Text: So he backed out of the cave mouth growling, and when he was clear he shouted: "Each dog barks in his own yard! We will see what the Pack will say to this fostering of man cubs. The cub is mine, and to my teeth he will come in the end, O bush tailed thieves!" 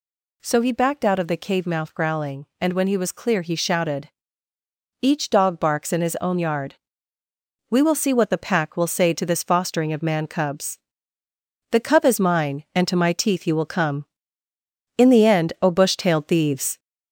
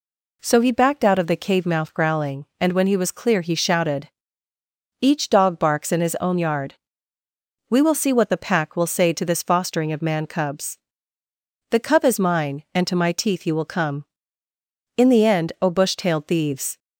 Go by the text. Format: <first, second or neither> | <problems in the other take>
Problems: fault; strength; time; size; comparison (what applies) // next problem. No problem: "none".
second | gets louder; throughout; 3.5 dB